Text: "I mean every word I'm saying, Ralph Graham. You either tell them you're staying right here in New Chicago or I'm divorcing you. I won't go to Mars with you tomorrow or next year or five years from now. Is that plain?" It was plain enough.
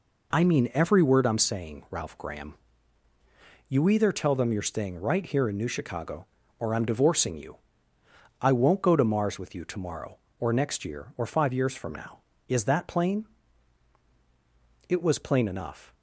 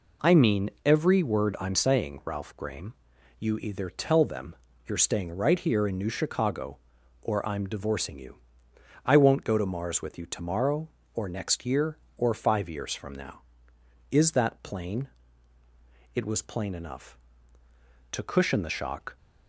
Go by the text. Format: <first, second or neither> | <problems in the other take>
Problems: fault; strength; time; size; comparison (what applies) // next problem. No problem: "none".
first | pauses between "mean" and "every"; slight; at 0.6 s; 0.16 s long // pauses between "them" and "you're"; slight; at 4.5 s; 0.32 s long // goes on to say "To cushion the shock"; noticeable; from 18.1 s on; 1.0 s long